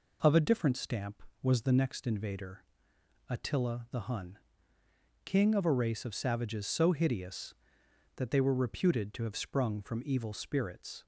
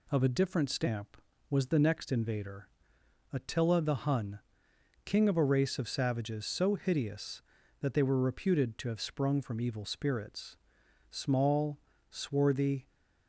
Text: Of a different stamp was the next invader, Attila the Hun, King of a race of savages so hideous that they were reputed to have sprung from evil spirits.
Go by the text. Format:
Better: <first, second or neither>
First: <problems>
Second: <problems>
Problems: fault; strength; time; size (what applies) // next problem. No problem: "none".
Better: first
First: none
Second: goes on to say "Small swarthy"; strong; from 11.1 s on; 1.7 s long